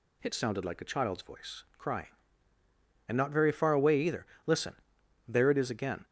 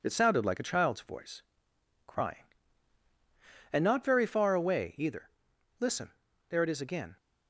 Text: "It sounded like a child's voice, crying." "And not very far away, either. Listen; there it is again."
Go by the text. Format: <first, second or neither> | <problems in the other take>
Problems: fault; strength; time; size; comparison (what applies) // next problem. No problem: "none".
first | gets quieter; slight; throughout; 3 dB